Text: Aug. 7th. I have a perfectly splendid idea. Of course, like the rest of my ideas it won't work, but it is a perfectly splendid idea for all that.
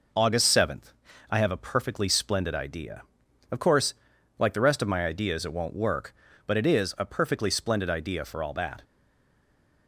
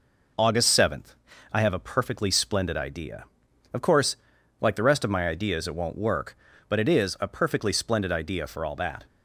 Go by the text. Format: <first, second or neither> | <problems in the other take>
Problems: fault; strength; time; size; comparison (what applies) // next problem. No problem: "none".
second | stays silent after the last word; from 8.8 s on; 1.0 s long